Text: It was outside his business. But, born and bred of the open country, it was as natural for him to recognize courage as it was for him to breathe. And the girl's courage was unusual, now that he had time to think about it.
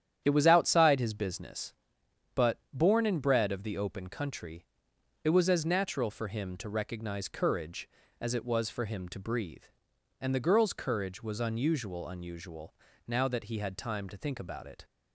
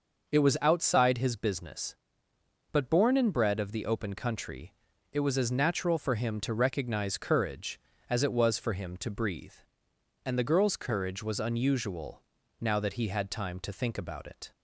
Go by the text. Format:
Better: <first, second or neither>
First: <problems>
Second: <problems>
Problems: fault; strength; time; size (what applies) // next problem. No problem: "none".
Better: second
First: starts louder than the rest; strong; until 1.2 s; 9.5 dB // says "unusual" twice; at 12.0 s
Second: none